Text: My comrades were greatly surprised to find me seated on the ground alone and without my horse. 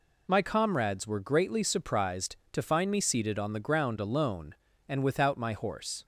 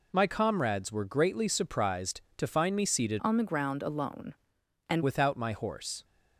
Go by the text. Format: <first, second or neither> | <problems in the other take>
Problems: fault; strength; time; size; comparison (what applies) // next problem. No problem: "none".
first | changes voice from "on" to "and"; from 3.1 to 5.0 s; 1.9 s long